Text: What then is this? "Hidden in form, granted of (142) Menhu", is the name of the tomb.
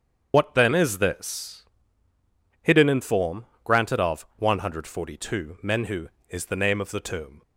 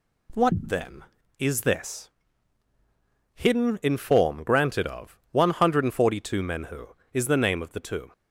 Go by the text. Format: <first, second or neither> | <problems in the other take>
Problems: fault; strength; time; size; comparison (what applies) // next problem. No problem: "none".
second | loses the start of "What"; at 0.3 s; 75 ms // starts louder than the rest; strong; until 1.3 s; 8 dB